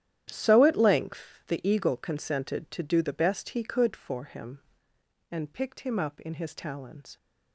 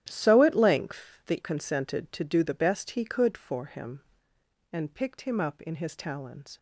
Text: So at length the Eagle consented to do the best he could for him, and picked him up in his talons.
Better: first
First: starts louder than the rest; strong; until 1.3 s; 11 dB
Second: starts louder than the rest; strong; until 1.1 s; 11 dB // skips "Eagle"; at 1.4 s

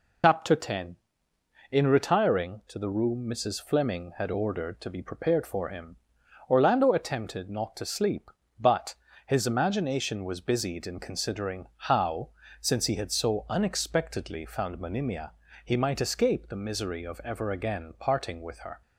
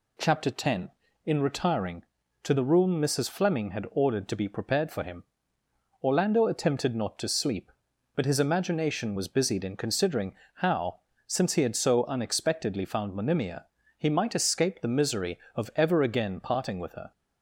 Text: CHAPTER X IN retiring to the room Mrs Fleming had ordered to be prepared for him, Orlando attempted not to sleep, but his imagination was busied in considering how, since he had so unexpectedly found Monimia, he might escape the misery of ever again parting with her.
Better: second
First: loses the start of "CHAPTER"; at 0.2 s; 95 ms // pauses between "but" and "his"; slight; at 8.9 s; 0.32 s long // pauses between "considering" and "how"; slight; at 11.6 s; 0.20 s long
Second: pauses between "considering" and "how"; slight; at 10.3 s; 0.22 s long

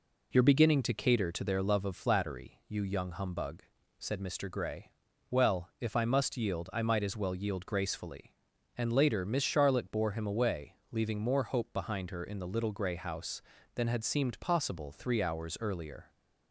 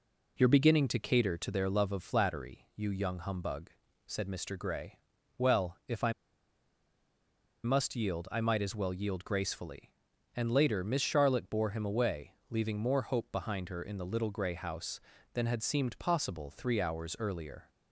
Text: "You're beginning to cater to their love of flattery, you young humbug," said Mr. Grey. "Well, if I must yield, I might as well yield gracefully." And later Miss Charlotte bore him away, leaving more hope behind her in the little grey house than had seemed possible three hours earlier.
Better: first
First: none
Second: pauses between "I" and "must"; strong; at 6.1 s; 1.5 s long

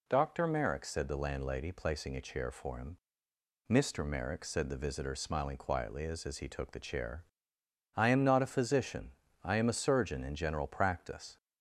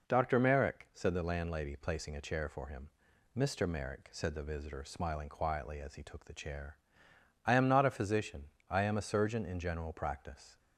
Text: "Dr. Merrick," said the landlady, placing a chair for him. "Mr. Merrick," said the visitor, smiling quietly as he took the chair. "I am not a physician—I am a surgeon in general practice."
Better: second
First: says "as" twice; at 6.2 s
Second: none

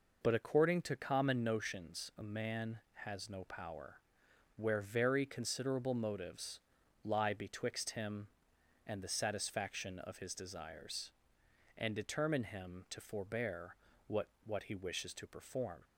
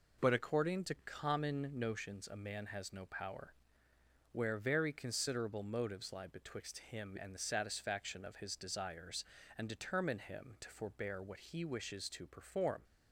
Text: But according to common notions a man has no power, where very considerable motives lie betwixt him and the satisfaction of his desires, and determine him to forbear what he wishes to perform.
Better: second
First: pauses between "motives" and "lie"; at 6.5 s; 0.44 s long // pauses between "forbear" and "what"; slight; at 13.7 s; 0.32 s long // says "what" twice; at 14.4 s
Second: none

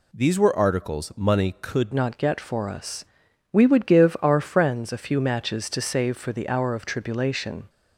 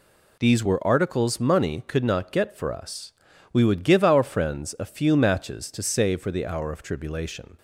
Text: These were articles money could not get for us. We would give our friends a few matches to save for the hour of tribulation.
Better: second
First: changes voice at "not"; from 1.9 s on; 5.7 s long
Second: none

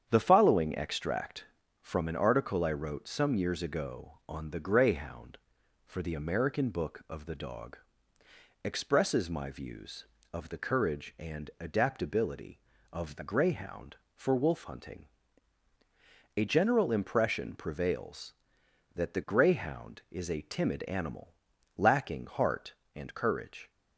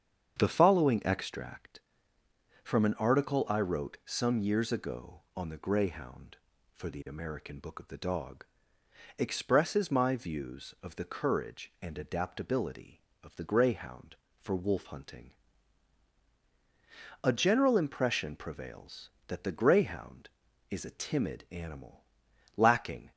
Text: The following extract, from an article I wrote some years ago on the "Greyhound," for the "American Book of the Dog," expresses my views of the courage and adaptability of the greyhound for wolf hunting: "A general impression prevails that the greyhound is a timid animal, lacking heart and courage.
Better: first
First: starts louder than the rest; strong; until 1.1 s; 8.5 dB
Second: starts louder than the rest; strong; until 1.4 s; 7.5 dB // stops before "heart and courage"; at 23.1 s

